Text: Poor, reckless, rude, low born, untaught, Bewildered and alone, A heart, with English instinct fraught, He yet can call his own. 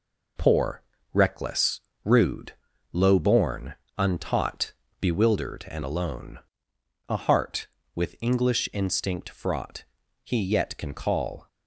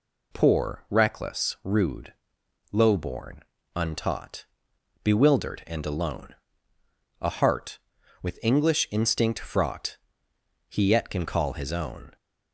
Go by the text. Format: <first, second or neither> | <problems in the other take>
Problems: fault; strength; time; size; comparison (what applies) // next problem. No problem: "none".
second | stops before "his own"; at 11.4 s